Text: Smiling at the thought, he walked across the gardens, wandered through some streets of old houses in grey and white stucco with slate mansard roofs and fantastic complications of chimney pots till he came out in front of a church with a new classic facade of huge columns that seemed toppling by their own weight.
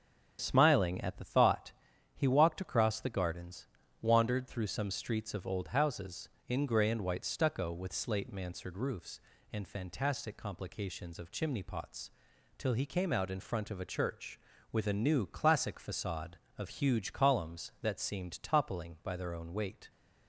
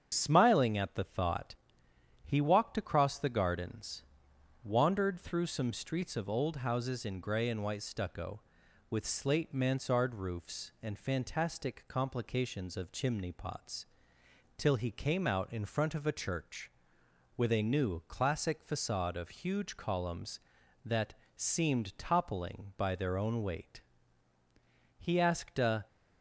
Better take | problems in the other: first | starts louder than the rest; strong; until 1.1 s; 8 dB; strong in the first // pauses between "pots" and "till"; noticeable; at 13.8 s; 0.72 s long; noticeable in the first // pauses between "that" and "seemed"; slight; at 21.1 s; 0.20 s long // goes on to say "He asked a"; noticeable; from 24.9 s on; 0.88 s long

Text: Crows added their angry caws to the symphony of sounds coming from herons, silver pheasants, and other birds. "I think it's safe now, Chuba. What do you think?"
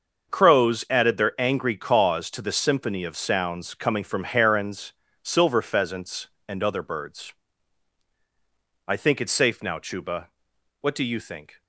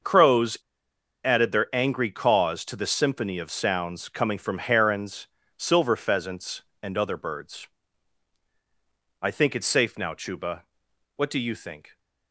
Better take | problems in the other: first | starts louder than the rest; until 1.7 s; 6.5 dB; also in the first // pauses between "Crows" and "added"; noticeable; at 0.5 s; 0.67 s long

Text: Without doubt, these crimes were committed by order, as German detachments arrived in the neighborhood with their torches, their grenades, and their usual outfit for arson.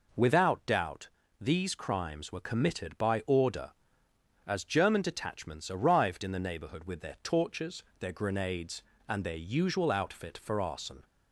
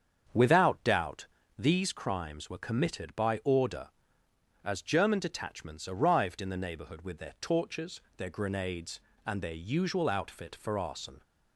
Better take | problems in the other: first | starts louder than the rest; strong; until 2.0 s; 7.5 dB

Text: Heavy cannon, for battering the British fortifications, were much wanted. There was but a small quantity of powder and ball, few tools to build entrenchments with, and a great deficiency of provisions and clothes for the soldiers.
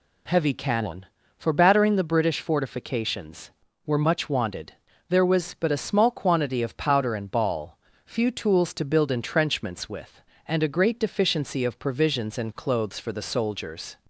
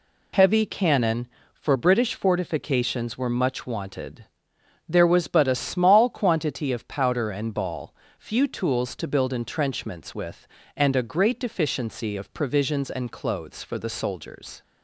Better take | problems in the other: first | skips "battering the"; at 1.7 s

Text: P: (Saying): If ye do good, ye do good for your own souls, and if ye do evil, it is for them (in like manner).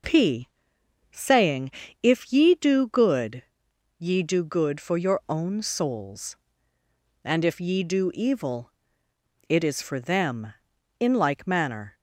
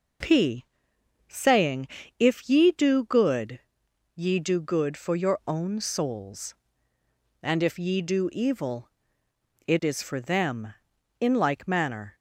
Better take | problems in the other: neither | none

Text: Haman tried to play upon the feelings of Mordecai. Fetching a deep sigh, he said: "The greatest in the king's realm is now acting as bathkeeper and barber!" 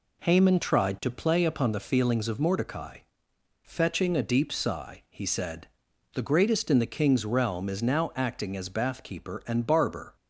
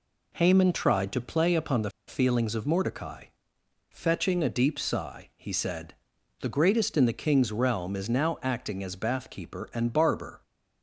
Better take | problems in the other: first | pauses between "the" and "feelings"; slight; at 1.9 s; 0.16 s long

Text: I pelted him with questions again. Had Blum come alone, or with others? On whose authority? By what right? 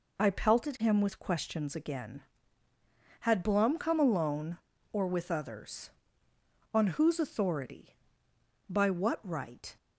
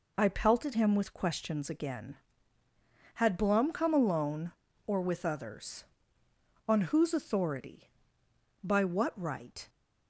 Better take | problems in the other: neither | none

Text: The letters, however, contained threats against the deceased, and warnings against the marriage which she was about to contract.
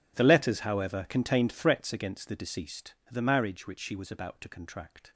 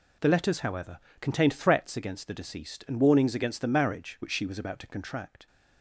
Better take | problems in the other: second | skips "and warnings against"; at 3.0 s

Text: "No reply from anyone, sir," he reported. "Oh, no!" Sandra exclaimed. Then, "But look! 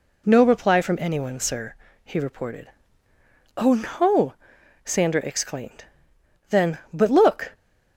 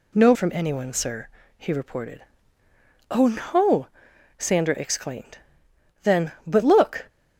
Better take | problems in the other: first | skips "reply"; at 0.3 s

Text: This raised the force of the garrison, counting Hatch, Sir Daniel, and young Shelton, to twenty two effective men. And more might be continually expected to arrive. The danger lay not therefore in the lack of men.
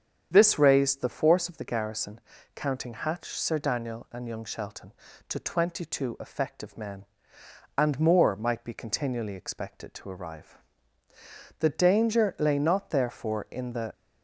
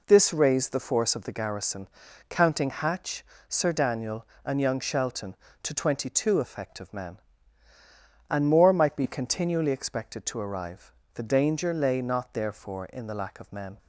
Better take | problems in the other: second | starts louder than the rest; strong; until 1.3 s; 8 dB // stops before "lack of men"; at 13.9 s

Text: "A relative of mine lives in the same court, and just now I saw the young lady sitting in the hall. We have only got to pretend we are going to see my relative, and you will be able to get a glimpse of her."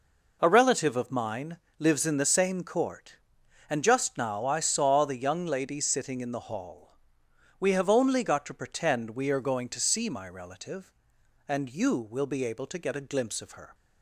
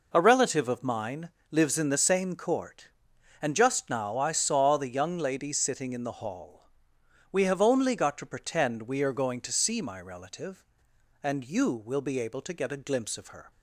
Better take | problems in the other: neither | pauses between "mine" and "lives"; slight; the same in both

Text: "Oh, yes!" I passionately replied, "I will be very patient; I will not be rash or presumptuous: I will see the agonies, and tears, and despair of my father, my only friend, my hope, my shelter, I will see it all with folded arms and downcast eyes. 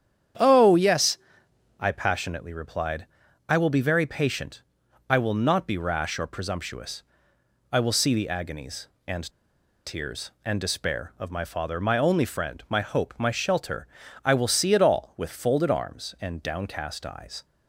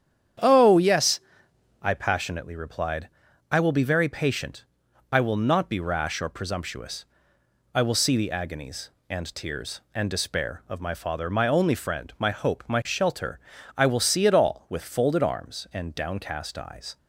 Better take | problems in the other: second | starts louder than the rest; strong; until 2.0 s; 9 dB; strong in the second // pauses between "and" and "tears"; noticeable; at 9.3 s; 0.53 s long

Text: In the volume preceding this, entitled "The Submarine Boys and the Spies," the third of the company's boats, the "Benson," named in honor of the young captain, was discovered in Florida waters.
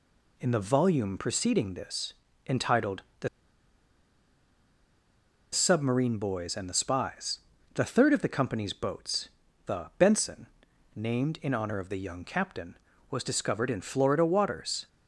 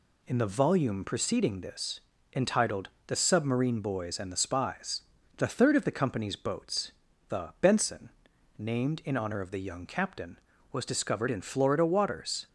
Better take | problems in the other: second | pauses between "entitled" and "The"; slight; at 3.0 s; 0.20 s long; slight in the second // pauses between "The" and "Submarine"; strong; at 3.2 s; 2.2 s long

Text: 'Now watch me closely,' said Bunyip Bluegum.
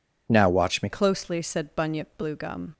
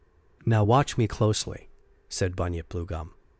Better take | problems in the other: second | changes voice at "closely"; from 0.8 s on; 1.9 s long

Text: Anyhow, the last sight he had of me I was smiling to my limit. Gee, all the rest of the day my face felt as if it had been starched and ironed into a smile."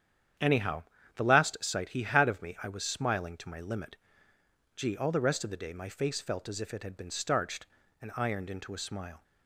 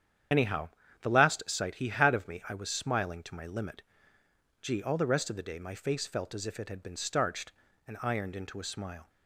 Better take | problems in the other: first | loses the start of "Anyhow"; at 0.3 s; 60 ms // starts louder than the rest; strong; until 1.6 s; 9 dB; strong in the first

